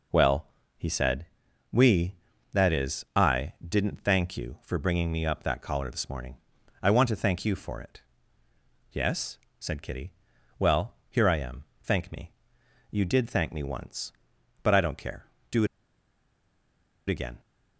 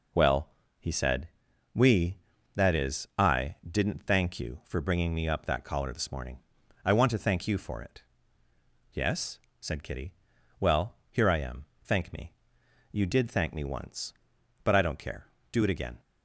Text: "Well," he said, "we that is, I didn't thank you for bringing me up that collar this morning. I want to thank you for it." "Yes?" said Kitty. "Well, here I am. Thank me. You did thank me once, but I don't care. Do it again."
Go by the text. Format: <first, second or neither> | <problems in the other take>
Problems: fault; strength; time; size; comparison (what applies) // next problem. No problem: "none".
second | pauses between "it" and "again"; strong; at 15.6 s; 1.4 s long